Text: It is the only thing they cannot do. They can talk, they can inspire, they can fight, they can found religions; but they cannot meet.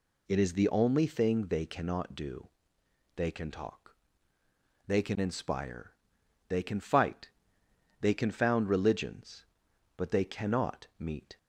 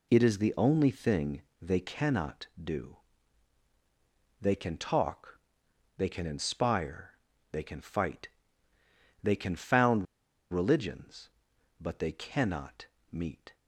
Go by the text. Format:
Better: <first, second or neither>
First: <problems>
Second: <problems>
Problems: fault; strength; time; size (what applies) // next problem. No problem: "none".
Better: first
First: none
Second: pauses between "thing" and "they"; slight; at 1.4 s; 0.20 s long // pauses between "found" and "religions"; noticeable; at 10.0 s; 0.47 s long // pauses between "cannot" and "meet"; slight; at 12.8 s; 0.26 s long